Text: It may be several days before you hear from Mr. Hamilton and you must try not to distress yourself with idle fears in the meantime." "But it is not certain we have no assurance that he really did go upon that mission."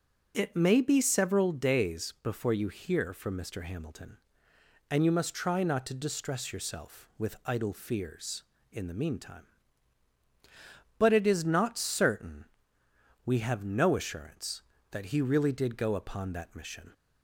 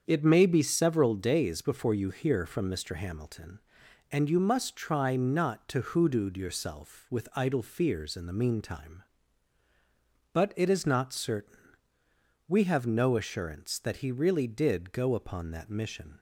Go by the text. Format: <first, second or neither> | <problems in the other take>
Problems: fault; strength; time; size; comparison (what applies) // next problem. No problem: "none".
first | starts louder than the rest; strong; until 1.0 s; 7 dB // says "hoodooed" for "distress"; at 5.8 s // pauses between "certain" and "we"; noticeable; at 11.5 s; 0.90 s long; noticeable in the first